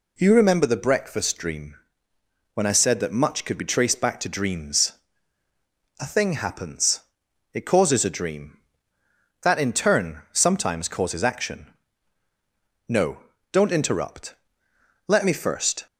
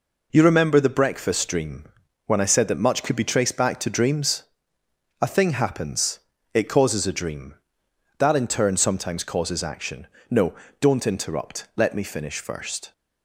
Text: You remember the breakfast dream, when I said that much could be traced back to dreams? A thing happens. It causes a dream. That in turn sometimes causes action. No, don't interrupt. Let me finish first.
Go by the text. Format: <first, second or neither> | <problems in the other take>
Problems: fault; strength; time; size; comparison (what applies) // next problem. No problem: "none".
second | skips "finish"; at 15.3 s